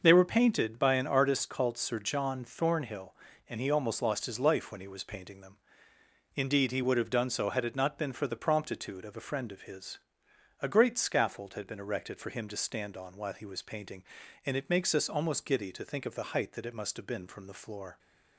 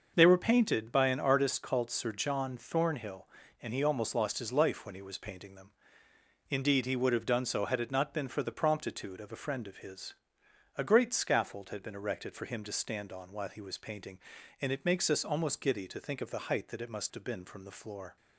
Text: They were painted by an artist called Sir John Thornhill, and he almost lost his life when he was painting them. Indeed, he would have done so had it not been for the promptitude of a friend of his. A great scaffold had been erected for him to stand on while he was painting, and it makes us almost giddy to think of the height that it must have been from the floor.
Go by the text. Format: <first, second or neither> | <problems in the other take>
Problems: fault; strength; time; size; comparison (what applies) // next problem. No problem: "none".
neither | starts louder than the rest; noticeable; the same in both